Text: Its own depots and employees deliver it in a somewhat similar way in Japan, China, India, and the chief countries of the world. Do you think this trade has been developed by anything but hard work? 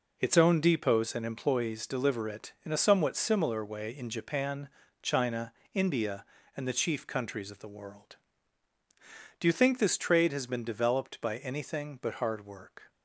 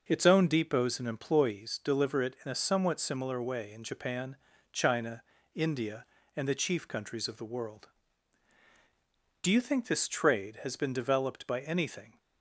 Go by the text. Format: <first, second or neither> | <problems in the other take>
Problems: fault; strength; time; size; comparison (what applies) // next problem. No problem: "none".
first | stops before "but hard work"; at 12.1 s